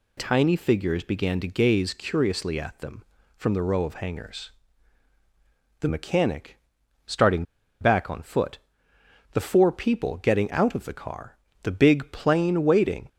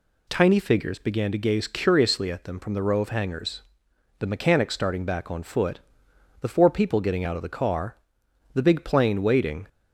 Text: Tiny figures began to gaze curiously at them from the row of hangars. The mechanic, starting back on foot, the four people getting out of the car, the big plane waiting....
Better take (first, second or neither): second